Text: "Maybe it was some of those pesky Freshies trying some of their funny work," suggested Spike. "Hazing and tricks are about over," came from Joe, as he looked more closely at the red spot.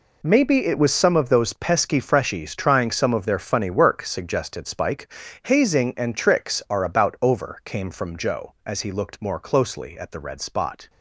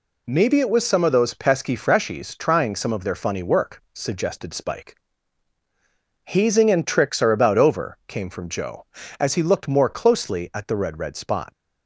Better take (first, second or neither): first